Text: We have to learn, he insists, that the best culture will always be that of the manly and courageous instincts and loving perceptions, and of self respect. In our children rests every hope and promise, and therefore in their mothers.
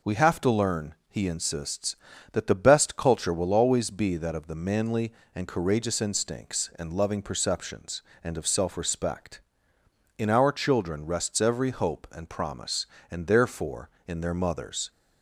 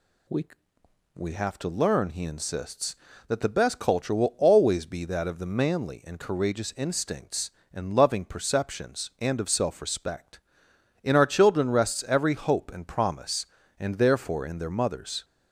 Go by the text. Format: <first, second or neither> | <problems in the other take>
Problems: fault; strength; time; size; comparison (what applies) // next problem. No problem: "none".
first | says "We" twice; at 1.1 s